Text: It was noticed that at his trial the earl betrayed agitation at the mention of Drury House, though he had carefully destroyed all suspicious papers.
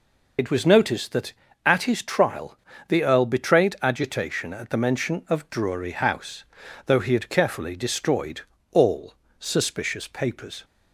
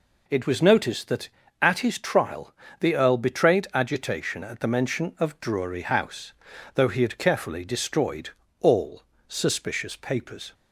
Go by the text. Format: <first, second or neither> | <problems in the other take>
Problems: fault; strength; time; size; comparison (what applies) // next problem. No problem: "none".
second | loses the start of "It"; at 0.3 s; 70 ms // pauses between "trial" and "the"; slight; at 2.5 s; 0.30 s long; slight in the second // pauses between "destroyed" and "all"; slight; at 8.4 s; 0.32 s long; slight in the second // pauses between "all" and "suspicious"; slight; at 9.1 s; 0.24 s long; slight in the second